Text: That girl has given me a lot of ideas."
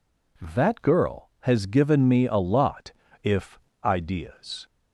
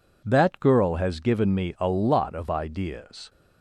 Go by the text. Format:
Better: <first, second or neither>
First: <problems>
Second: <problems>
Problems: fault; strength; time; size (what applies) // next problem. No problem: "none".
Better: second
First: says "if" for "of"; at 3.2 s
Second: none